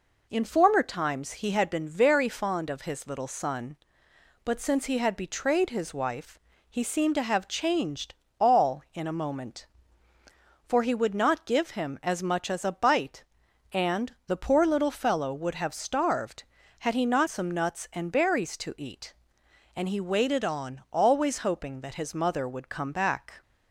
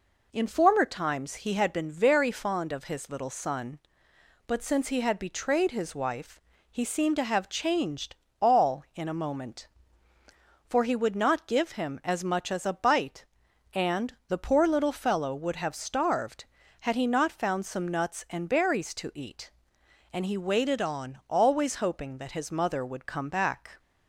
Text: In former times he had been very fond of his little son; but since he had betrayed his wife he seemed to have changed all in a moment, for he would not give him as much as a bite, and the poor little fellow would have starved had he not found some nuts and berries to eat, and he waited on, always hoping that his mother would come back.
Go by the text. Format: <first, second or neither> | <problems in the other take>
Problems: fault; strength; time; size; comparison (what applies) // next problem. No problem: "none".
second | pauses between "wife" and "he"; slight; at 6.3 s; 0.28 s long; slight in the second // pauses between "changed" and "all"; slight; at 8.1 s; 0.26 s long; slight in the second // skips "found"; at 17.2 s